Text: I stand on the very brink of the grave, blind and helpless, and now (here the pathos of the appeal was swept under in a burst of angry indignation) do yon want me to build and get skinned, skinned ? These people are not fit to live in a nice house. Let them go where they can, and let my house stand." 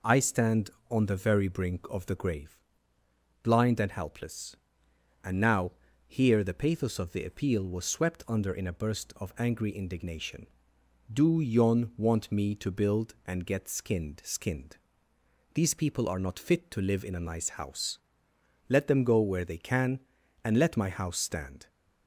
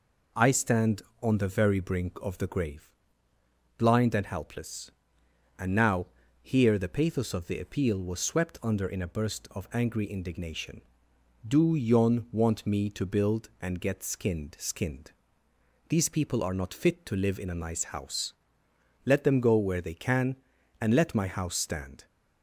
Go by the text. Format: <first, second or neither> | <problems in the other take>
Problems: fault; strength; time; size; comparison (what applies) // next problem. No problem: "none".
neither | none